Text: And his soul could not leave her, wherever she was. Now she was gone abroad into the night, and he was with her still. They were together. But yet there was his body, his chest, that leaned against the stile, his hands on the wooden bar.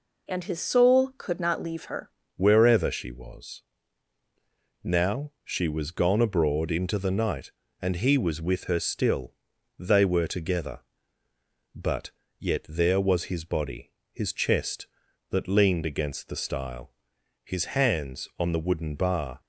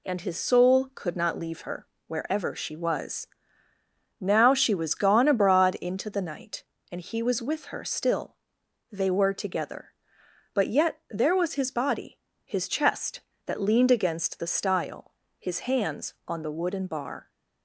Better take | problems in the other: second | changes voice at "wherever"; from 2.3 s on; 17.0 s long // pauses between "But" and "yet"; slight; at 12.0 s; 0.30 s long

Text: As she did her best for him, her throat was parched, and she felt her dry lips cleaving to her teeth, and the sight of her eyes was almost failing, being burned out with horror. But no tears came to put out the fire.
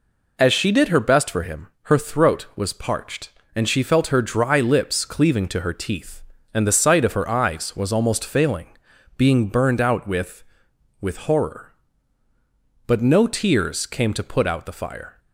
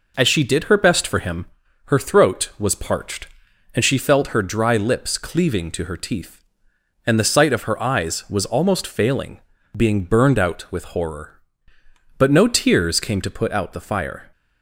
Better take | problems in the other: second | says "with" twice; at 11.0 s

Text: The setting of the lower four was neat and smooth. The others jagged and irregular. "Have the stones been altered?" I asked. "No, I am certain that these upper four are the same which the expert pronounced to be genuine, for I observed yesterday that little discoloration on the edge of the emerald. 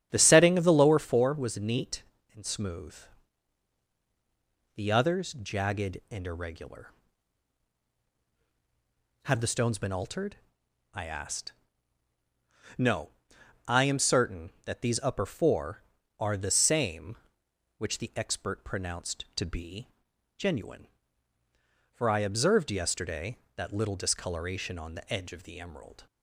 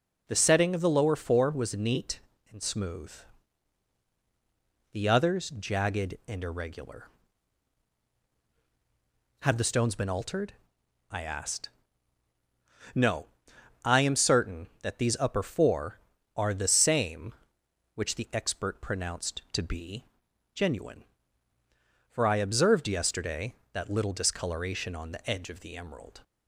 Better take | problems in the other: second | starts louder than the rest; strong; until 1.2 s; 9.5 dB // pauses between "be" and "genuine"; noticeable; at 19.8 s; 0.50 s long; noticeable in the second

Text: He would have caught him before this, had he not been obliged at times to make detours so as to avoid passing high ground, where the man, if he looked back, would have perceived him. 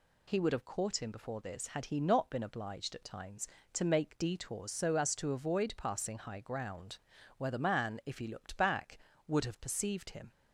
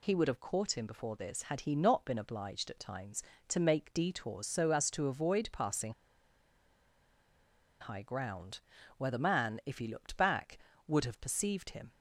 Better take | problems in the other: first | pauses between "passing" and "high"; strong; at 5.9 s; 1.8 s long

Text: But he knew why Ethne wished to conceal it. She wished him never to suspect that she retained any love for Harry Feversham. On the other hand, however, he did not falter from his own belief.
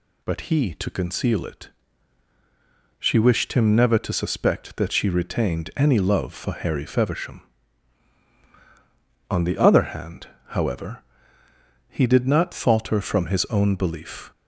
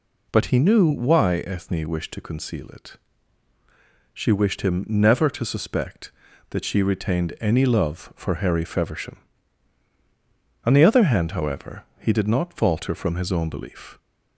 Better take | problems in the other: second | skips "knew why Ethne wished"; at 0.7 s

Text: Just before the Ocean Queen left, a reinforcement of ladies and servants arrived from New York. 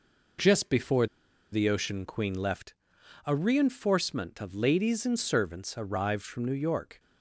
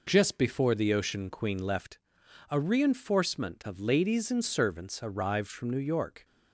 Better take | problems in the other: second | pauses between "before" and "the"; noticeable; at 1.0 s; 0.46 s long

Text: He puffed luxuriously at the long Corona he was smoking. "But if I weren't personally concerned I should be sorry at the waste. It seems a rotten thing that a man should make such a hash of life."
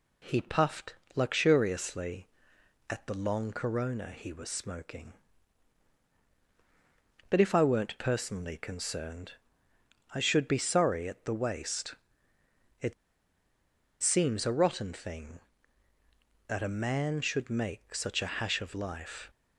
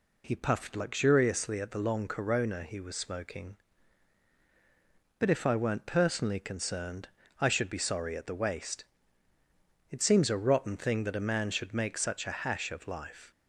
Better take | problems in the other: second | pauses between "puffed" and "luxuriously"; slight; at 0.9 s; 0.20 s long // pauses between "concerned" and "I"; noticeable; at 9.3 s; 0.82 s long; slight in the second // pauses between "It" and "seems"; at 12.9 s; 1.0 s long

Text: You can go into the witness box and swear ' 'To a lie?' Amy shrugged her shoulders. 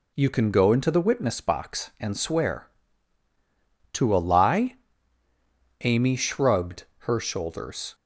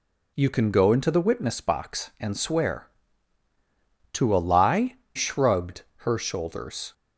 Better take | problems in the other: first | skips "Amy"; at 5.0 s // pauses between "shrugged" and "her"; slight; at 5.8 s; 0.26 s long; slight in the first

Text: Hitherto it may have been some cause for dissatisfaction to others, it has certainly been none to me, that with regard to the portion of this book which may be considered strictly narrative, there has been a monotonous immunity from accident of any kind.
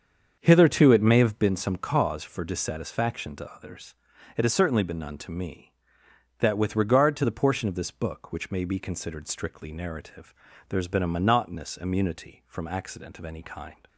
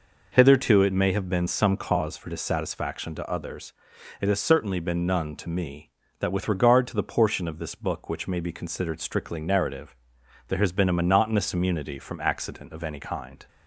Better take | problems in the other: second | starts louder than the rest; until 1.6 s; 7 dB

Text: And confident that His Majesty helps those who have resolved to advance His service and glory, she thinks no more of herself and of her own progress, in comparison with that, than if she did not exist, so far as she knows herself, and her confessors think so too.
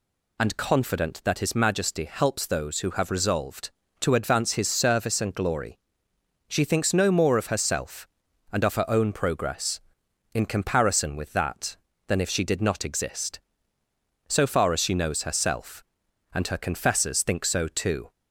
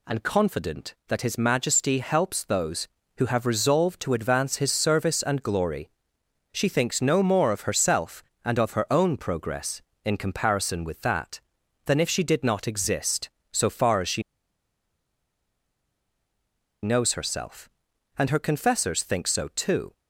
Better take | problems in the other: first | pauses between "she" and "knows"; strong; at 14.2 s; 2.6 s long

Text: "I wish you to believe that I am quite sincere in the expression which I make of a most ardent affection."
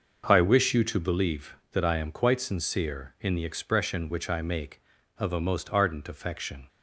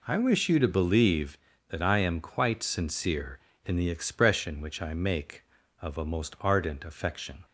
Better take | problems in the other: second | starts louder than the rest; noticeable; until 1.2 s; 6 dB

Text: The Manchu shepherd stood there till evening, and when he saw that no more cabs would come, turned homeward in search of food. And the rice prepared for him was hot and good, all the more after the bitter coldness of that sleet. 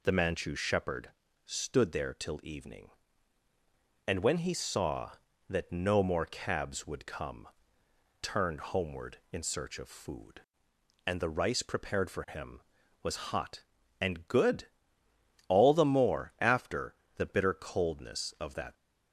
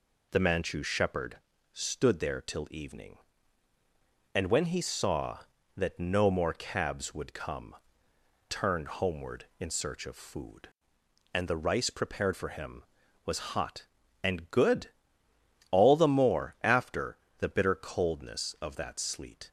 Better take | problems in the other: second | pauses between "shepherd" and "stood"; slight; at 1.0 s; 0.34 s long; slight in the second // pauses between "after" and "the"; slight; at 16.9 s; 0.20 s long; slight in the second // stops before "sleet"; at 18.7 s

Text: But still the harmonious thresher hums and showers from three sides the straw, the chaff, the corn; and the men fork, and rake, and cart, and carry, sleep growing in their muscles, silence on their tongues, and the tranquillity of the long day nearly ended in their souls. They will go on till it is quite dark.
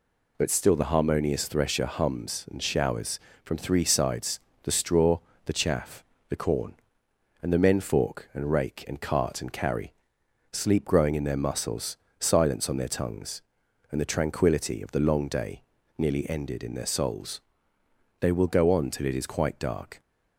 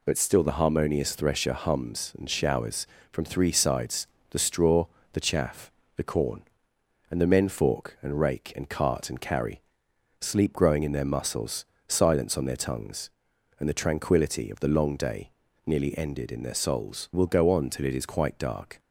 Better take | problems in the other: first | pauses between "sides" and "the"; slight; at 4.0 s; 0.24 s long; slight in the first // pauses between "day" and "nearly"; slight; at 15.3 s; 0.36 s long; slight in the first // skips "They"; at 17.1 s

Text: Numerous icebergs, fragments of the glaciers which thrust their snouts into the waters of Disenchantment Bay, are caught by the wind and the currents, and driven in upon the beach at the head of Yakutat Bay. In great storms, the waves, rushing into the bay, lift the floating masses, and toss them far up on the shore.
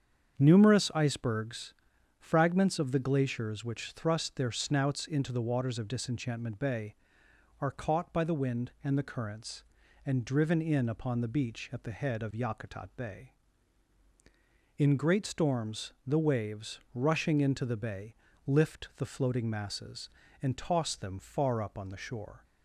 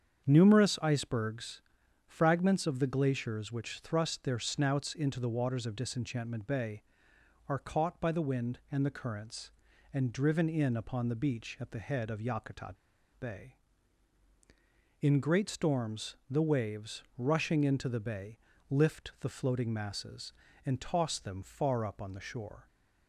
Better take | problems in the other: first | starts louder than the rest; strong; until 1.2 s; 7.5 dB; strong in the first // pauses between "Yakutat" and "Bay"; at 12.7 s; 0.43 s long

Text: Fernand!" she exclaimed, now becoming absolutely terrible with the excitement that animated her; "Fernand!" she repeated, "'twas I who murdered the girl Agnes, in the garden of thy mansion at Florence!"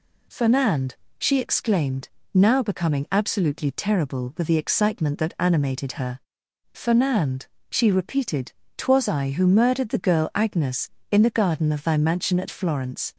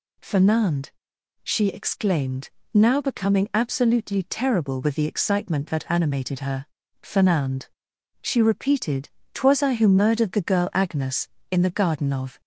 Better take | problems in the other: first | stops before "thy mansion at Florence"; at 12.4 s

